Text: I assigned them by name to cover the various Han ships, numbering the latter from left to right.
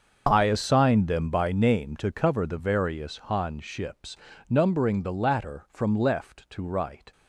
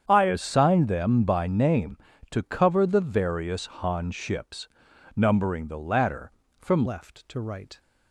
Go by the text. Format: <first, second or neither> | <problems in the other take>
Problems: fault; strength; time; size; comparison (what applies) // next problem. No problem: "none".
first | starts louder than the rest; strong; until 1.0 s; 8 dB; also in the first // pauses between "various" and "Han"; slight; at 3.6 s; 0.16 s long // changes voice at "left"; from 6.8 s on; 0.9 s long